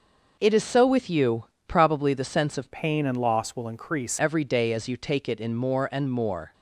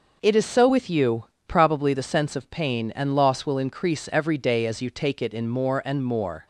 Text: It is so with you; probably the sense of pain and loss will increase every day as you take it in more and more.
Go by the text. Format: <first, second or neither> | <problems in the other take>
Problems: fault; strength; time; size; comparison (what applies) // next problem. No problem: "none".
second | changes voice from "pain" to "increase"; from 2.7 to 4.1 s; 1.4 s long